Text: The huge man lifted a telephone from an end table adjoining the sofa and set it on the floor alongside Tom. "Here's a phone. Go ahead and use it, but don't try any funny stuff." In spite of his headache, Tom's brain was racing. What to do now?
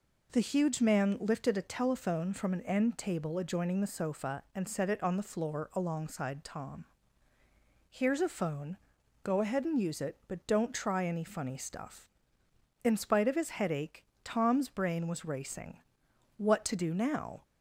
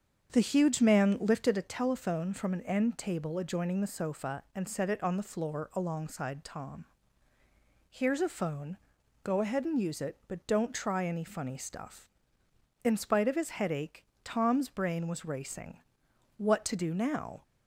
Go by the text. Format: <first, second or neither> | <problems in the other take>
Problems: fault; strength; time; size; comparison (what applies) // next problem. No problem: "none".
first | starts louder than the rest; strong; until 1.7 s; 7 dB